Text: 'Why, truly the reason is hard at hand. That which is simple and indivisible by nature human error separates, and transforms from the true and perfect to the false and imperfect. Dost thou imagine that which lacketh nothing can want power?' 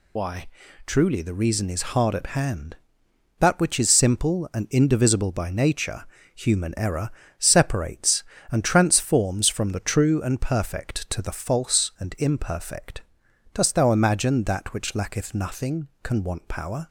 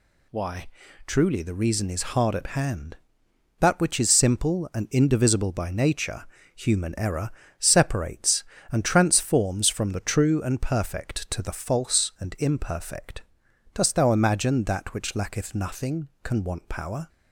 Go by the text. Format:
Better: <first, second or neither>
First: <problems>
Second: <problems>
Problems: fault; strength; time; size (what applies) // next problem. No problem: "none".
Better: second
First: loses the start of "Why"; at 0.1 s; 55 ms // pauses between "nature" and "human"; slight; at 6.0 s; 0.34 s long // pauses between "error" and "separates"; slight; at 7.0 s; 0.28 s long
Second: pauses between "nature" and "human"; slight; at 6.2 s; 0.34 s long // pauses between "error" and "separates"; slight; at 7.3 s; 0.28 s long